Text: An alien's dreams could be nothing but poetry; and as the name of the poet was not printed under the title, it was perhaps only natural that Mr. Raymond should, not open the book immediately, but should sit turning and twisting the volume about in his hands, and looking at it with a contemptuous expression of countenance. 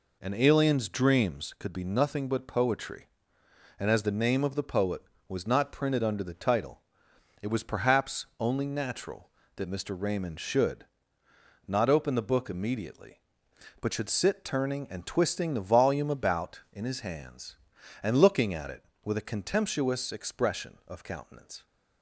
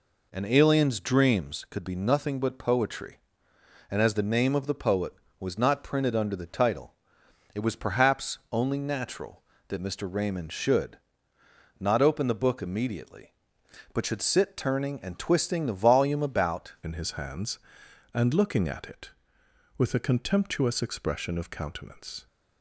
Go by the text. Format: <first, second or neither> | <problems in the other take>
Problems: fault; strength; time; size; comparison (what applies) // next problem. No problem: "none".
first | changes voice at "in"; from 16.8 s on; 5.4 s long